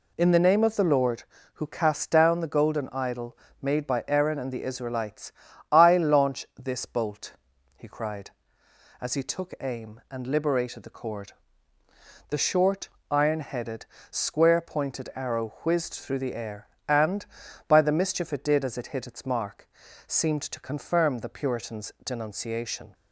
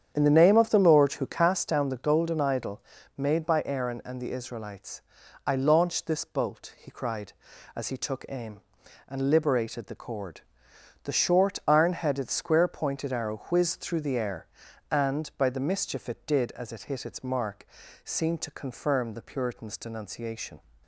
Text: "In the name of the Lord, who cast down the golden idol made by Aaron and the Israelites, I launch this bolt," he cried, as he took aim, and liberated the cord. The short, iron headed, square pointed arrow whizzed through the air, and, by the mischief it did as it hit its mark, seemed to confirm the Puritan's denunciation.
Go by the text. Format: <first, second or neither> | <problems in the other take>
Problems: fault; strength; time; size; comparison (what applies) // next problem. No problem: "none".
first | starts louder than the rest; strong; until 1.7 s; 8.5 dB // pauses between "idol" and "made"; slight; at 2.8 s; 0.34 s long; slight in the first